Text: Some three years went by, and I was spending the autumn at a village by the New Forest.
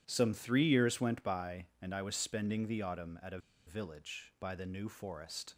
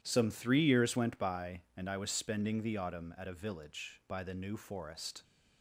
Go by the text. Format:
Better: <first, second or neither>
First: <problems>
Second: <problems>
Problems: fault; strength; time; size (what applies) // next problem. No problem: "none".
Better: second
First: pauses between "a" and "village"; slight; at 3.3 s; 0.28 s long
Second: none